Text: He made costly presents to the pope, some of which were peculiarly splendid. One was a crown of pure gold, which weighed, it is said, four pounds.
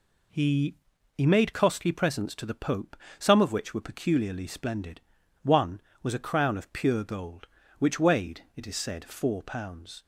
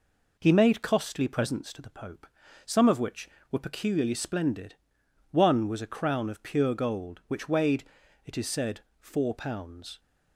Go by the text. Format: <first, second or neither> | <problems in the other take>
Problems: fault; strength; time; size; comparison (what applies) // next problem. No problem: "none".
second | says "He" twice; at 1.1 s